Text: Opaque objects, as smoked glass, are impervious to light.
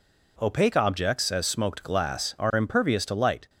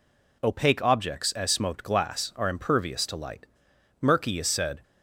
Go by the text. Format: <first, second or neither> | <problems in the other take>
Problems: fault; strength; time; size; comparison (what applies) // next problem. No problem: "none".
first | goes on to say "Murky is said"; noticeable; from 4.0 s on; 0.80 s long